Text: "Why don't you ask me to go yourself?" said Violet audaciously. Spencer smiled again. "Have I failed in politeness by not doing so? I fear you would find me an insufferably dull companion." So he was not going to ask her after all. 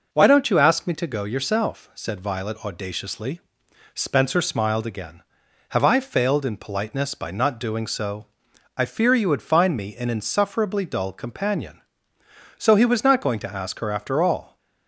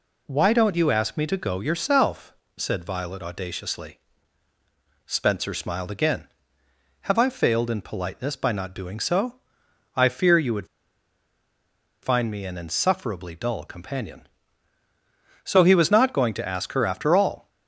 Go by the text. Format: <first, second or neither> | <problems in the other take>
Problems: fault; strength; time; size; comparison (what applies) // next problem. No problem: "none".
first | pauses between "would" and "find"; strong; at 10.6 s; 1.3 s long